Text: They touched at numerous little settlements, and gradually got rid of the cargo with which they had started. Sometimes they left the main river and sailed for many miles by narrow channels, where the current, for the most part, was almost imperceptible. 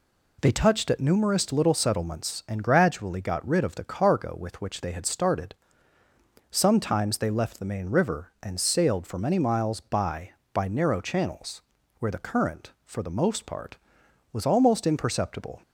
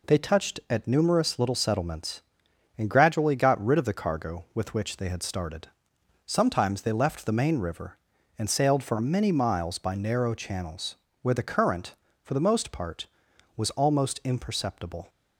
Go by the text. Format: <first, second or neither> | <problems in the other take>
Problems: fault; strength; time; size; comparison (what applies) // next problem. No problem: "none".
second | says "by" twice; at 10.5 s